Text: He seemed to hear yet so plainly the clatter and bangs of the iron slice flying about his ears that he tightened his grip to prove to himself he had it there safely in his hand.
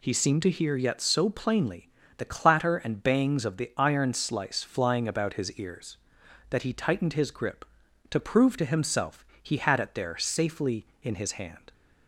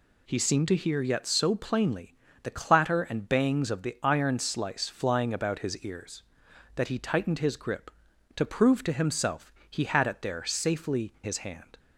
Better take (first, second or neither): first